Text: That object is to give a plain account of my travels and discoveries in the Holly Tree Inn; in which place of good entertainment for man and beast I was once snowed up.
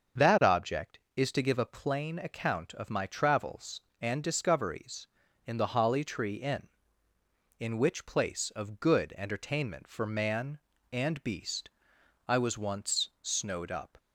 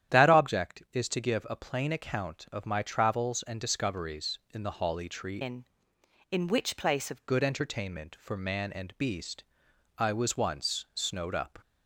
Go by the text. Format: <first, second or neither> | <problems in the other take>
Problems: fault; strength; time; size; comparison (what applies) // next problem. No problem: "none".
first | starts louder than the rest; strong; until 1.2 s; 10.5 dB; also in the first // changes voice from "Inn" to "of"; from 5.4 to 7.2 s; 1.8 s long // pauses between "beast" and "I"; noticeable; at 9.4 s; 0.54 s long; noticeable in the first